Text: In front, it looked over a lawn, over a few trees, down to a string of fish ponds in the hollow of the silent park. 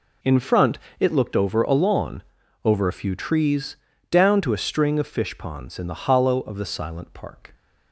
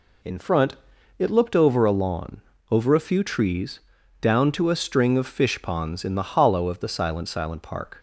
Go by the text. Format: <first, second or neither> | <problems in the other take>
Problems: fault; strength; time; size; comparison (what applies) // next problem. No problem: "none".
first | says "silent" twice; at 7.2 s